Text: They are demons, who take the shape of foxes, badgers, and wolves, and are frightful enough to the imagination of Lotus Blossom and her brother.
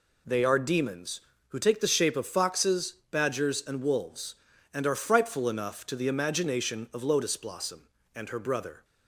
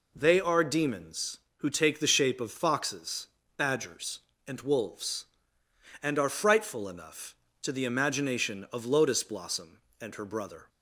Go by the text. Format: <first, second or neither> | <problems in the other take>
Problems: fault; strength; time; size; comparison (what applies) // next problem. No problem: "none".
neither | none